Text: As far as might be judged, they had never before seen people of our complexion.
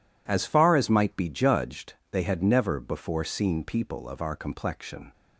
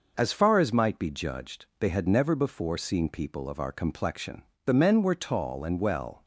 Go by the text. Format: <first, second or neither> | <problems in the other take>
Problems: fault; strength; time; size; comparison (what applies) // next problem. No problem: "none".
first | goes on to say "The men were tall and well"; from 4.6 s on; 1.6 s long